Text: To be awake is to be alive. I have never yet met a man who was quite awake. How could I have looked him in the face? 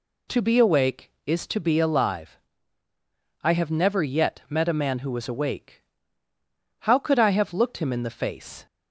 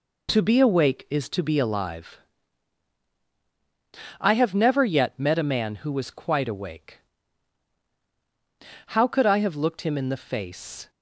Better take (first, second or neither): second